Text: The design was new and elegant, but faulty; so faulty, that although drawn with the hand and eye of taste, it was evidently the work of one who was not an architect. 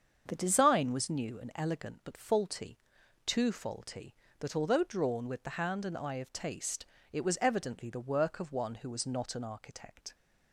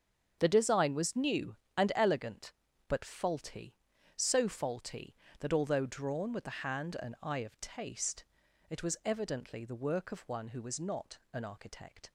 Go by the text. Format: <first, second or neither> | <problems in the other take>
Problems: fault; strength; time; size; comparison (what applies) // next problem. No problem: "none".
second | starts louder than the rest; strong; until 1.2 s; 7 dB; strong in the second // says "too" for "so"; at 3.2 s